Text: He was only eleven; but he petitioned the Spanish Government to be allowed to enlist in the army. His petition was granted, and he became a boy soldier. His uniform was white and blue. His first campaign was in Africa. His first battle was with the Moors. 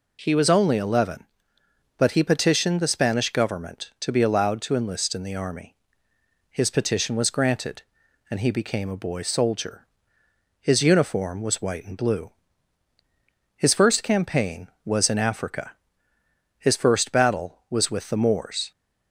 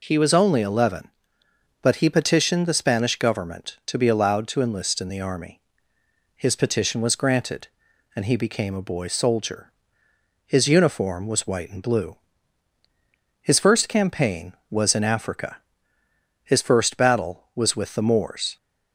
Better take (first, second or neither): neither